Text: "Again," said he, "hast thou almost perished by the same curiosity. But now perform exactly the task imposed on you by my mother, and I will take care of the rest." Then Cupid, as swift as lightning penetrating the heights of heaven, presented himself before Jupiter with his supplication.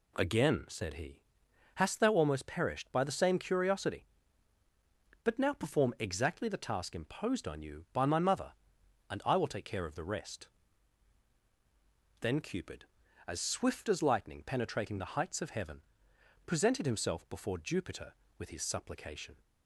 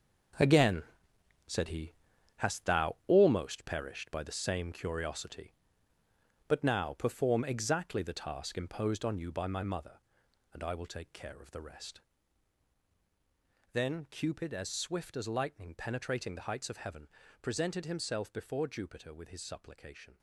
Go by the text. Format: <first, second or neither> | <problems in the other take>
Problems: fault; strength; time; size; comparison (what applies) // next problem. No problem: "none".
first | gets quieter; strong; throughout; 10 dB